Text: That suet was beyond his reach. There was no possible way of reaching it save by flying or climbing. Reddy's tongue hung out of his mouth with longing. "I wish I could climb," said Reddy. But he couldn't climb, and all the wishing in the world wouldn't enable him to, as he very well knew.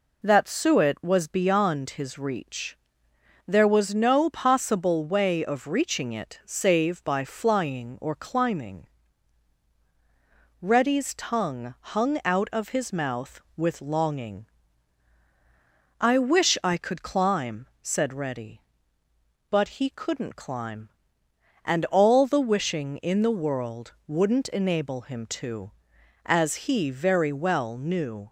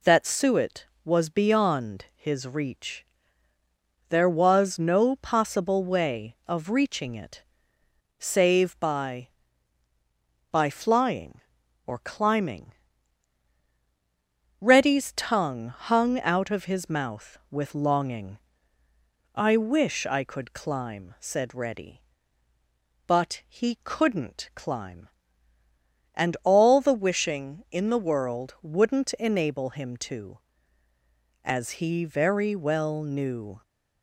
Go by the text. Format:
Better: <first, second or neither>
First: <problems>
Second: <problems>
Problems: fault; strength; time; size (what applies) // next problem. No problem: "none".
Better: first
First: none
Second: pauses between "it" and "save"; noticeable; at 7.4 s; 0.74 s long // says "by" twice; at 10.4 s